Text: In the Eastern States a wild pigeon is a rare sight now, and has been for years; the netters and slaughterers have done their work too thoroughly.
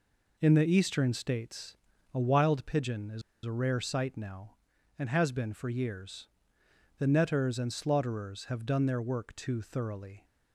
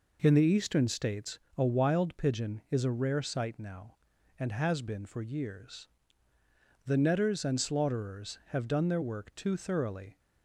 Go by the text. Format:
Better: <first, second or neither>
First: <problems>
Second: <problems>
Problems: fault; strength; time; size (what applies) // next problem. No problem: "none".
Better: second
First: pauses between "States" and "a"; slight; at 1.7 s; 0.36 s long // pauses between "is" and "a"; slight; at 3.2 s; 0.22 s long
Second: pauses between "States" and "a"; slight; at 1.3 s; 0.18 s long